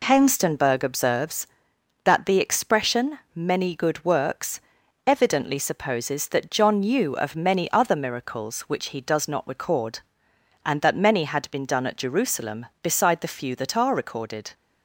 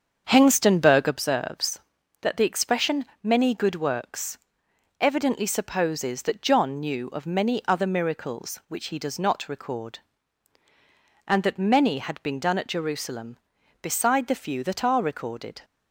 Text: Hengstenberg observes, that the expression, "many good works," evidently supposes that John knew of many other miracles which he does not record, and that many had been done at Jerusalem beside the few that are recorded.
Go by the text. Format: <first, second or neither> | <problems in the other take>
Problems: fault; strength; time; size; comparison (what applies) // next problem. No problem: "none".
first | starts louder than the rest; until 1.3 s; 7 dB